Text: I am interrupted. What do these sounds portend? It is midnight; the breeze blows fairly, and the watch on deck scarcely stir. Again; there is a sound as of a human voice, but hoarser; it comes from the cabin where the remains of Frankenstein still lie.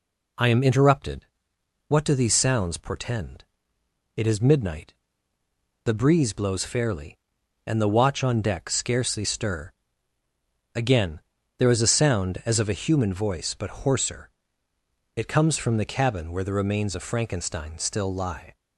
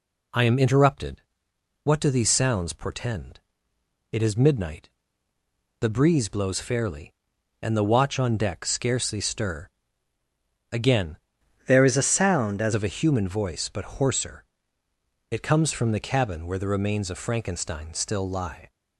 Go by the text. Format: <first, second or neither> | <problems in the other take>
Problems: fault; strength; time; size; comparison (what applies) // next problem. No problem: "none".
first | changes voice from "there" to "as"; from 11.6 to 12.7 s; 1.1 s long